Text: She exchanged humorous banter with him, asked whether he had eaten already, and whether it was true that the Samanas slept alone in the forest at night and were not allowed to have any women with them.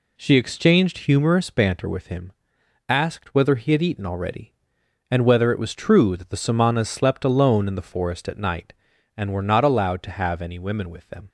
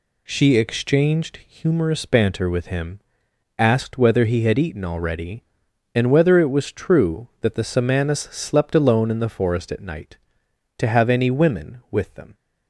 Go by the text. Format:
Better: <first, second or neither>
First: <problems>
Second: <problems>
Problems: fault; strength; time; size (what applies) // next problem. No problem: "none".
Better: first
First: none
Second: skips "and were not allowed"; at 10.4 s